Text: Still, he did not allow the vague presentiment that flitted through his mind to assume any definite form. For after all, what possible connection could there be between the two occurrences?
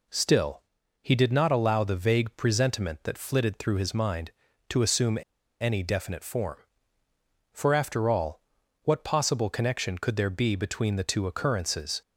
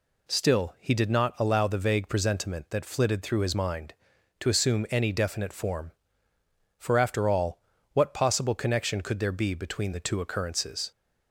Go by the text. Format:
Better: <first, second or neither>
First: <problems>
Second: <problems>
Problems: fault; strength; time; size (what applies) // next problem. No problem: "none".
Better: second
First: pauses between "assume" and "any"; at 5.1 s; 0.42 s long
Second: none